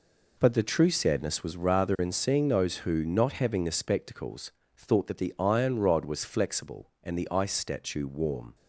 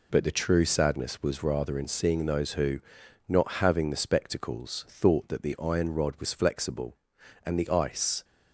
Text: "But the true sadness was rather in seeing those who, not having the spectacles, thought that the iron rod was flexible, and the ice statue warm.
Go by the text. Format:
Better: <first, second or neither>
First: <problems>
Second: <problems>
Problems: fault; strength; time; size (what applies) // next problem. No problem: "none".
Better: first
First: none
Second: stops before "statue warm"; at 8.2 s